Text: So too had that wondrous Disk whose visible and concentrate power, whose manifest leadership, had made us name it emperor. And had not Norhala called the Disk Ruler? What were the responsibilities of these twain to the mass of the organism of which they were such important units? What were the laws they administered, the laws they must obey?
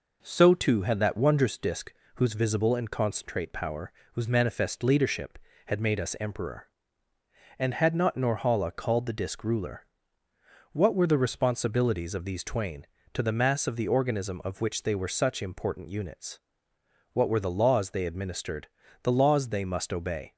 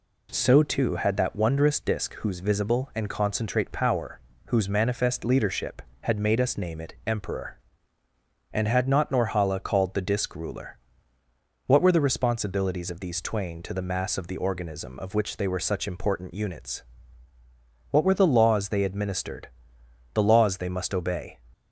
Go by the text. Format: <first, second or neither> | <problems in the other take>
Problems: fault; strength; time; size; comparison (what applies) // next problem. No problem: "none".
second | pauses between "Disk" and "whose"; slight; at 1.9 s; 0.22 s long // skips "name it"; at 6.1 s